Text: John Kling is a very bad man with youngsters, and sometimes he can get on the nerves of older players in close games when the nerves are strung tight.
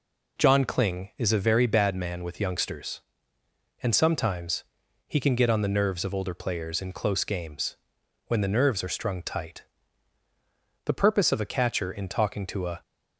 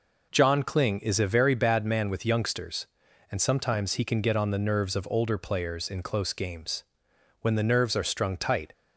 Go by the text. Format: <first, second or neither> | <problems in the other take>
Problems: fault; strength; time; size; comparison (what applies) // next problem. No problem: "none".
second | pauses between "sometimes" and "he"; at 4.6 s; 0.44 s long // pauses between "games" and "when"; noticeable; at 7.7 s; 0.52 s long; noticeable in the second // goes on to say "The purpose of a catcher in talking to a"; strong; from 10.8 s on; 1.9 s long